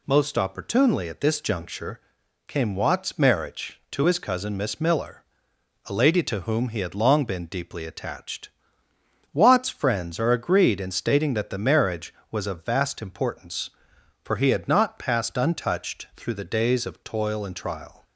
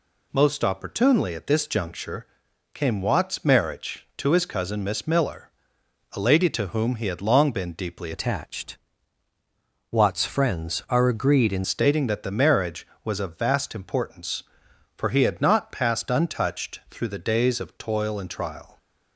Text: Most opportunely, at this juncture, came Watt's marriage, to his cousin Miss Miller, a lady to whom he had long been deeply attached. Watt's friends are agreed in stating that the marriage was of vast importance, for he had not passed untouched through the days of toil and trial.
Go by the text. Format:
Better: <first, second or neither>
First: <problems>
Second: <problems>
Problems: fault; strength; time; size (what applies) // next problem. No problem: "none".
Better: first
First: none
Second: changes voice from "attached" to "in"; from 8.1 to 11.6 s; 3.5 s long